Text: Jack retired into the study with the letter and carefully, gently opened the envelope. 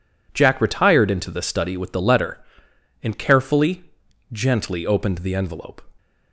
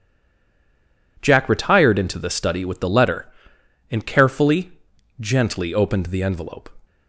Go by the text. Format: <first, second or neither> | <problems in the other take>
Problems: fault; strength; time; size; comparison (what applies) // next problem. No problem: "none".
first | stays silent before the first word; until 1.1 s; 1.1 s long